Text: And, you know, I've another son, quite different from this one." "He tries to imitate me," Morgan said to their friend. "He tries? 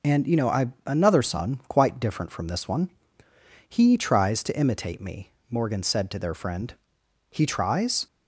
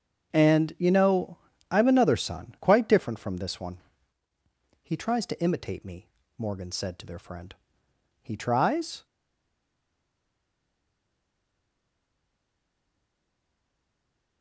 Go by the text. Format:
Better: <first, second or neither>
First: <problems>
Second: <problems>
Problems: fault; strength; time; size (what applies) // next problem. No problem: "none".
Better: first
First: none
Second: starts louder than the rest; until 1.3 s; 7 dB // stays silent after the last word; strong; from 9.0 s on; 5.4 s long